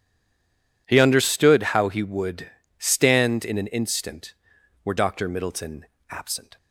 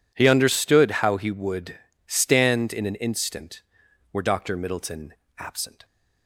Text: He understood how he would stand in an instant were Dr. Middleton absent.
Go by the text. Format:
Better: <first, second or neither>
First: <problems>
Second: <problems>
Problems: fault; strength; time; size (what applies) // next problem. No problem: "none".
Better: second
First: stays silent before the first word; slight; until 0.8 s; 0.8 s long // pauses between "would" and "stand"; slight; at 2.4 s; 0.30 s long // pauses between "Middleton" and "absent"; slight; at 5.8 s; 0.26 s long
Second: pauses between "would" and "stand"; slight; at 1.7 s; 0.30 s long // pauses between "Middleton" and "absent"; slight; at 5.1 s; 0.26 s long